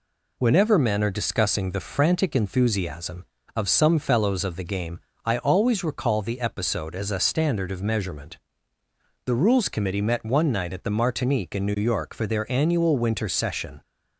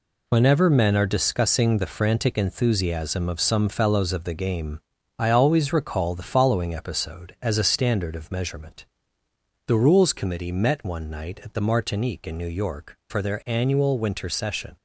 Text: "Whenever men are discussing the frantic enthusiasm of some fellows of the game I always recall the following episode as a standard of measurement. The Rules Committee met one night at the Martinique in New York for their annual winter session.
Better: second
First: pauses between "game" and "I"; slight; at 4.9 s; 0.26 s long // skips "following"; at 6.3 s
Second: pauses between "game" and "I"; slight; at 4.8 s; 0.36 s long

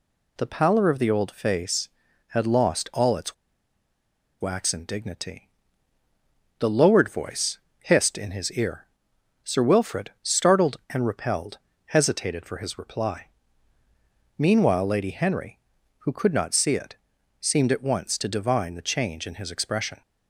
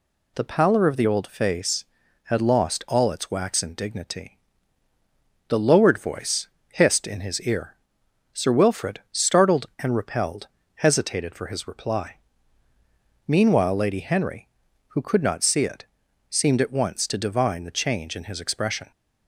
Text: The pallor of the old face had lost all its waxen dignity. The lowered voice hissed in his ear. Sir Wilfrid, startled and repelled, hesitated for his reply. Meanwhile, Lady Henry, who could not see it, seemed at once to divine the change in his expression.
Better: second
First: pauses between "its" and "waxen"; at 3.3 s; 1.0 s long // pauses between "voice" and "hissed"; slight; at 7.5 s; 0.22 s long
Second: pauses between "voice" and "hissed"; slight; at 6.4 s; 0.22 s long

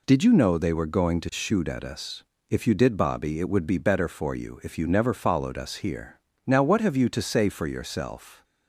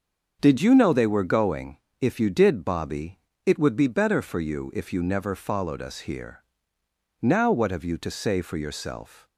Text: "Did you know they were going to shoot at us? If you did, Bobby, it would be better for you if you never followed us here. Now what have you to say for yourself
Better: first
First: none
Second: starts louder than the rest; until 1.4 s; 6.5 dB // skips "to shoot at us"; at 1.8 s

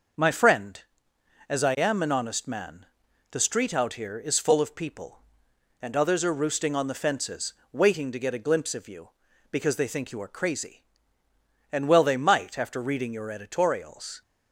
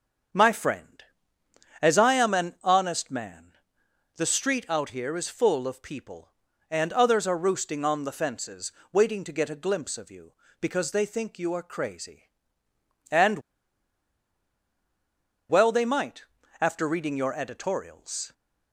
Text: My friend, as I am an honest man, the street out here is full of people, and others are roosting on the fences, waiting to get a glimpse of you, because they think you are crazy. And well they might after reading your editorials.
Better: first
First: starts louder than the rest; until 1.9 s; 6.5 dB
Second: starts louder than the rest; until 2.1 s; 7 dB // pauses between "And" and "well"; strong; at 13.3 s; 2.1 s long // pauses between "might" and "after"; slight; at 16.2 s; 0.36 s long

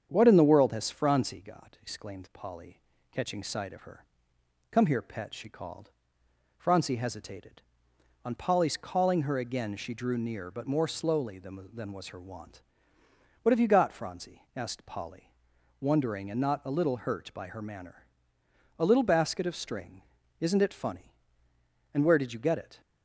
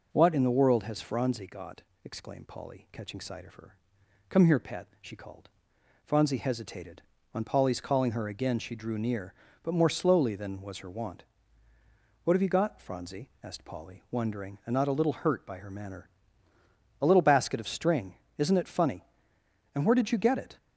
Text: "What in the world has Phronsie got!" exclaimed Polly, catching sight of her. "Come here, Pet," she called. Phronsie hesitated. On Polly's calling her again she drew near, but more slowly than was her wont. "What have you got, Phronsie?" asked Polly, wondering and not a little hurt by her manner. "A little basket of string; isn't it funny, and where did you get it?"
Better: second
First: starts louder than the rest; strong; until 1.1 s; 8 dB // says "than" twice; at 11.7 s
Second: none

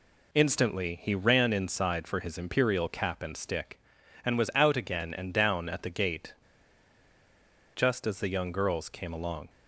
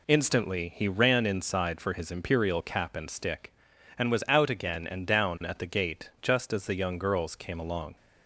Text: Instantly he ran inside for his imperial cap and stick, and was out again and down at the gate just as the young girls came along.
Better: second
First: pauses between "gate" and "just"; strong; at 6.3 s; 1.4 s long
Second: none

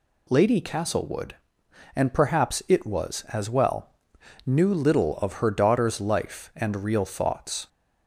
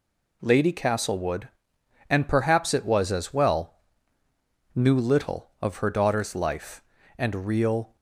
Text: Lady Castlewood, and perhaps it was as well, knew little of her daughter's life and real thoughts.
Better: first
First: none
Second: stops before "thoughts"; at 7.9 s

